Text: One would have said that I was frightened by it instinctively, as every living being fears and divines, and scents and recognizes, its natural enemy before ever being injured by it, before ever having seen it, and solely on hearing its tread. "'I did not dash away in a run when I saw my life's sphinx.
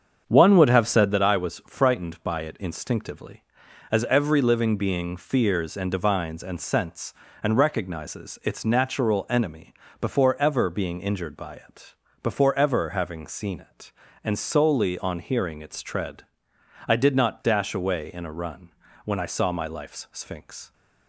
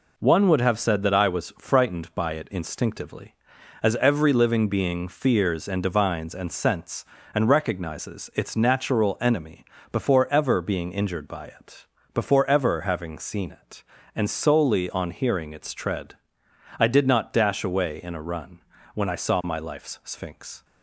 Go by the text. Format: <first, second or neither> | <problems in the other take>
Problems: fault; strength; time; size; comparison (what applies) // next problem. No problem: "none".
second | starts louder than the rest; strong; until 1.2 s; 7.5 dB // pauses between "enemy" and "before"; slight; at 9.7 s; 0.26 s long; slight in the second // pauses between "run" and "when"; slight; at 18.7 s; 0.34 s long; slight in the second